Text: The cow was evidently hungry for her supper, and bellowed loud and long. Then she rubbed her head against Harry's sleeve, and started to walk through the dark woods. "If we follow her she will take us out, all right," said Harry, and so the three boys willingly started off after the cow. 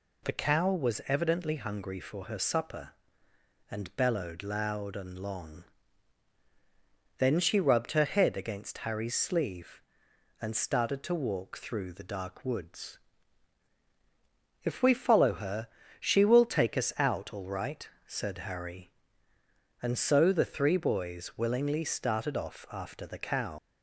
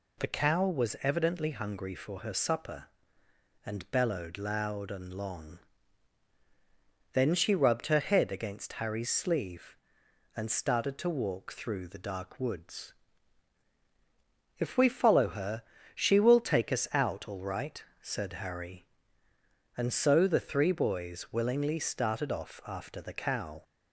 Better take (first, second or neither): second